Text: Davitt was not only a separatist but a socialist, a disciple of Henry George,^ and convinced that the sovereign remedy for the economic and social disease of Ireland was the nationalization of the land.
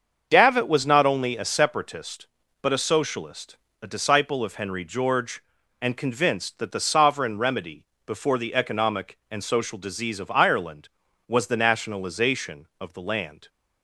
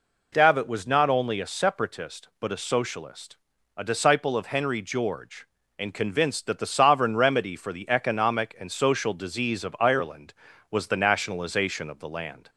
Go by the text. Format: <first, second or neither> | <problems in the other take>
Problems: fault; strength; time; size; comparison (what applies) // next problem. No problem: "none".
second | starts louder than the rest; until 1.3 s; 6.5 dB // says "before" for "for"; at 8.0 s